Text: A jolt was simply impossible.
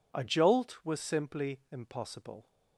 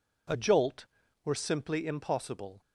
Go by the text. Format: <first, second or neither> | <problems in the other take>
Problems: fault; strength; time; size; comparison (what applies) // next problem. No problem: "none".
first | says "were" for "was"; at 1.2 s